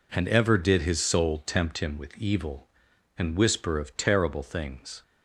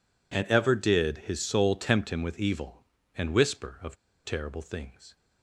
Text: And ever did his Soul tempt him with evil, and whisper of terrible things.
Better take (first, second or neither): first